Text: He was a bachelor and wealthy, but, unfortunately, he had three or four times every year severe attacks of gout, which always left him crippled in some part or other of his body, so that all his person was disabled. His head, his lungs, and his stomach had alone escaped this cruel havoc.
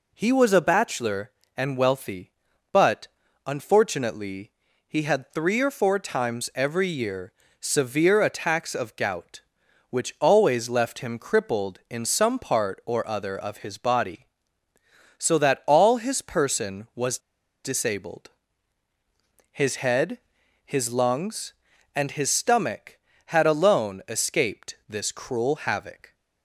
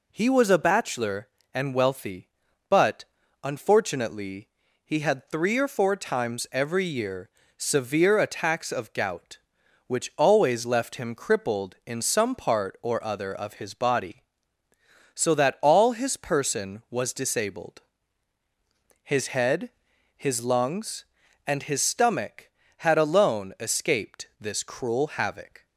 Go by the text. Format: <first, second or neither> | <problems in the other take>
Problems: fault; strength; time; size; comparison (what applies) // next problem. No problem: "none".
second | pauses between "year" and "severe"; slight; at 7.3 s; 0.28 s long; slight in the second // pauses between "was" and "disabled"; noticeable; at 17.1 s; 0.46 s long